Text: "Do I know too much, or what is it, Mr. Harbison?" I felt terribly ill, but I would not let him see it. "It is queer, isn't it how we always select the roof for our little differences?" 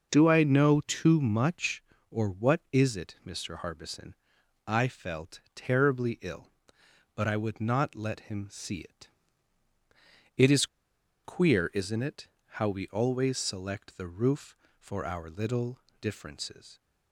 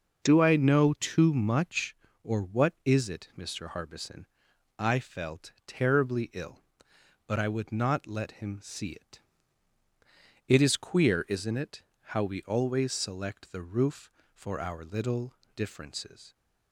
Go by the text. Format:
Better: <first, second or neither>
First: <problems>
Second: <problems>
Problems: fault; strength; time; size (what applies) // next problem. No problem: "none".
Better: second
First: pauses between "felt" and "terribly"; slight; at 5.3 s; 0.16 s long // pauses between "is" and "queer"; noticeable; at 10.6 s; 0.58 s long // pauses between "it" and "how"; slight; at 12.2 s; 0.32 s long // pauses between "little" and "differences"; slight; at 15.7 s; 0.22 s long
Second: pauses between "felt" and "terribly"; slight; at 5.4 s; 0.16 s long // pauses between "it" and "how"; slight; at 11.8 s; 0.32 s long // pauses between "little" and "differences"; slight; at 15.3 s; 0.22 s long